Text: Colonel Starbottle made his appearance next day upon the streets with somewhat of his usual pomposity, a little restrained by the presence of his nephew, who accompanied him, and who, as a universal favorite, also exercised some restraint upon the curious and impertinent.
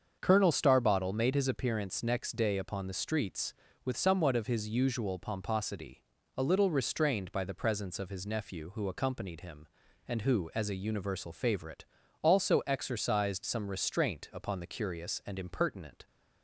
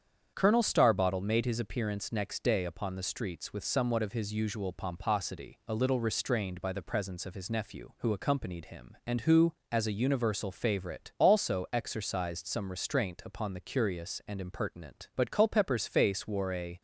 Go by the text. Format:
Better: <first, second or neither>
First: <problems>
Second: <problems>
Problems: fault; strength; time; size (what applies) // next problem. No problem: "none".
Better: first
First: starts louder than the rest; until 1.2 s; 7 dB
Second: starts louder than the rest; strong; until 1.3 s; 8 dB // goes on to say "But Culpepper's face wore a"; from 15.1 s on; 1.6 s long